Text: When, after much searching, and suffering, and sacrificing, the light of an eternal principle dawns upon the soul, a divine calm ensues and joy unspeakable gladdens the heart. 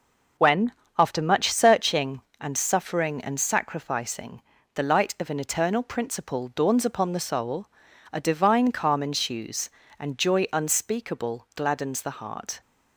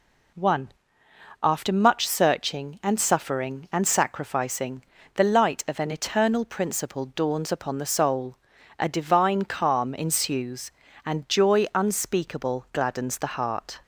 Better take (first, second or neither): first